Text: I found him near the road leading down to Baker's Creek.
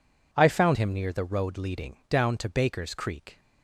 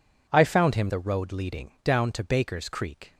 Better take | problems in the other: first | skips "near"; at 0.8 s

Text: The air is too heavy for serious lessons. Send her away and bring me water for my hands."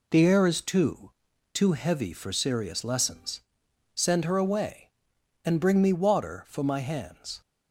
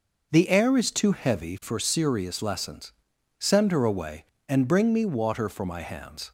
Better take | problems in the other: second | says "too" twice; at 1.5 s

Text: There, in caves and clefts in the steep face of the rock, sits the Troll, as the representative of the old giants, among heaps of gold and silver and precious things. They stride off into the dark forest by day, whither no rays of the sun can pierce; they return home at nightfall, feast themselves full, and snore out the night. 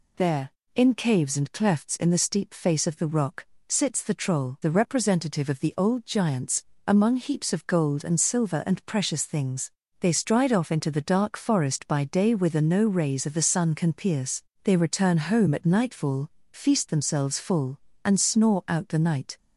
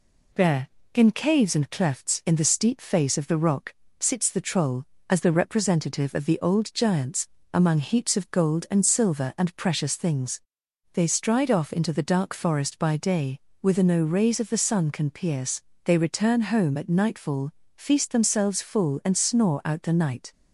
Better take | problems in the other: second | skips "as"; at 4.6 s

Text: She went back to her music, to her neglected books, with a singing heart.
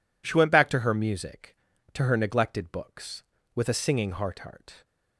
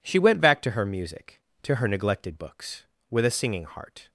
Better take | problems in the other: second | says "heart" twice; at 4.3 s

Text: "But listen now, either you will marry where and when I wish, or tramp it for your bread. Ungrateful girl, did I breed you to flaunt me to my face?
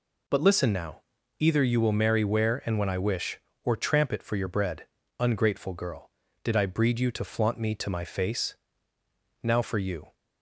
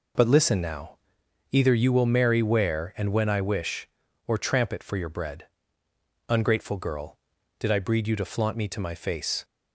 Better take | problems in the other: second | goes on to say "Now for you"; noticeable; from 9.4 s on; 0.72 s long

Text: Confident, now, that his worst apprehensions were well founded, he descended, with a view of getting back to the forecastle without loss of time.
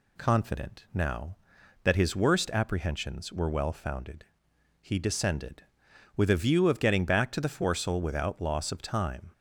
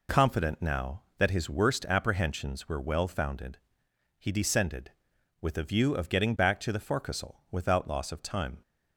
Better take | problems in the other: neither | none

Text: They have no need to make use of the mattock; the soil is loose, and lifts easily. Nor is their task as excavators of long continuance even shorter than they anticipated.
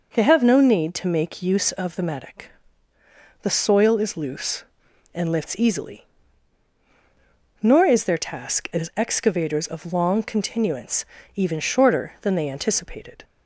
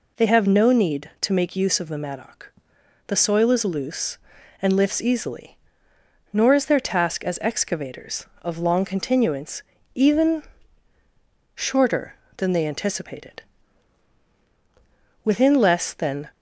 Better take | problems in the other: first | pauses between "continuance" and "even"; slight; at 9.6 s; 0.32 s long; slight in the first // pauses between "even" and "shorter"; at 10.4 s; 1.1 s long // goes on to say "Within less than"; noticeable; from 15.2 s on; 1.0 s long

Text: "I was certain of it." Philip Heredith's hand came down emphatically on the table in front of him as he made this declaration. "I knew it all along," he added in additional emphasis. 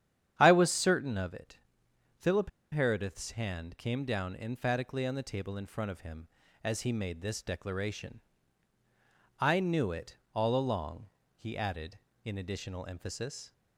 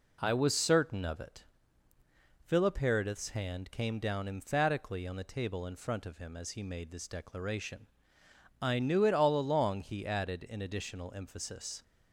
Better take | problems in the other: second | starts louder than the rest; strong; until 1.3 s; 9.5 dB // pauses between "Philip" and "Heredith's"; slight; at 2.4 s; 0.22 s long // pauses between "it" and "all"; slight; at 10.1 s; 0.16 s long

